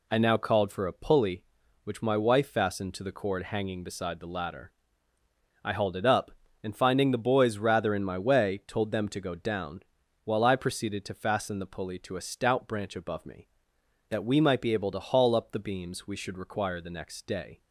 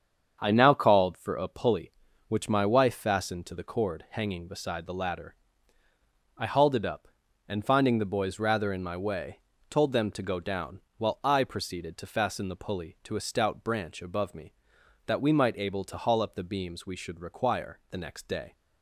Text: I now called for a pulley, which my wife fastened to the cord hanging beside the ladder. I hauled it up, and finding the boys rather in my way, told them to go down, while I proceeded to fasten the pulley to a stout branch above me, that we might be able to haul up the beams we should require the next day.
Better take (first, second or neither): first